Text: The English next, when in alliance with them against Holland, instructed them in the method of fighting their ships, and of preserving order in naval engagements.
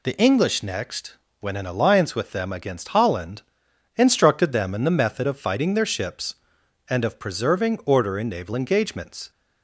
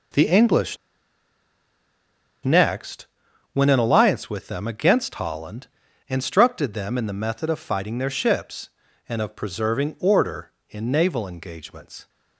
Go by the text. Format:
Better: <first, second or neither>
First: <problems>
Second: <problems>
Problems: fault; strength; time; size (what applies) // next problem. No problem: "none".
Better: first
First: none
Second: pauses between "English" and "next"; strong; at 0.7 s; 1.6 s long